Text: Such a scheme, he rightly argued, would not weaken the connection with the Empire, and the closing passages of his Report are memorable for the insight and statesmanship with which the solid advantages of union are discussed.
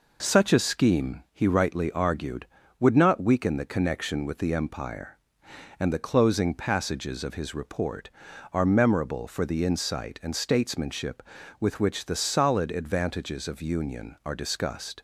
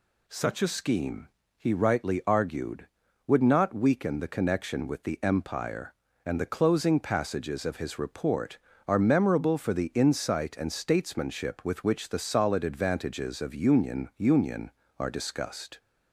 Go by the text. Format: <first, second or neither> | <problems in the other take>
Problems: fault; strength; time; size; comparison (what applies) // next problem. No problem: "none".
first | says "union" twice; at 14.1 s